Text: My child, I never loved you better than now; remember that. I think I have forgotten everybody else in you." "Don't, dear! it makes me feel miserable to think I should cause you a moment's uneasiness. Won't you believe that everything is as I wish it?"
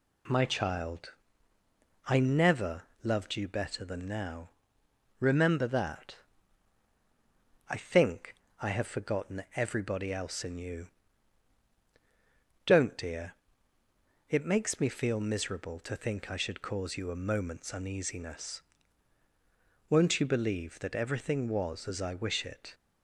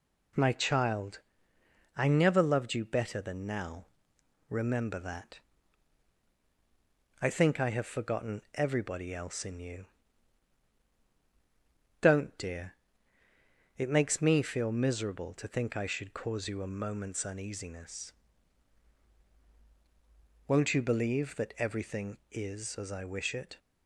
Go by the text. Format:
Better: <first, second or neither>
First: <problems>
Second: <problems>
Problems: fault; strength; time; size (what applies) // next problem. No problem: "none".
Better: second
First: pauses between "never" and "loved"; slight; at 2.8 s; 0.22 s long // pauses between "think" and "I"; slight; at 8.3 s; 0.26 s long // says "was" for "is"; at 21.4 s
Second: none